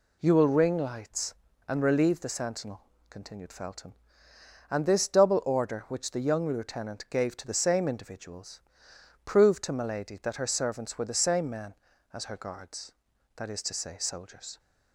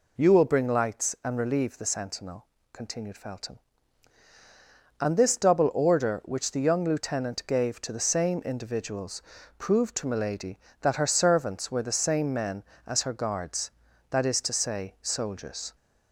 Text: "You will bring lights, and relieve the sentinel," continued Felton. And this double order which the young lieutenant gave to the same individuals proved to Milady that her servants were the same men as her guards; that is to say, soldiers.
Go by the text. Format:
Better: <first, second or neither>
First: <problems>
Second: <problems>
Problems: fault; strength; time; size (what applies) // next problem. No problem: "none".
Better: second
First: says "ring" for "bring"; at 0.4 s // pauses between "individuals" and "proved"; noticeable; at 8.6 s; 0.64 s long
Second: pauses between "individuals" and "proved"; at 9.2 s; 0.38 s long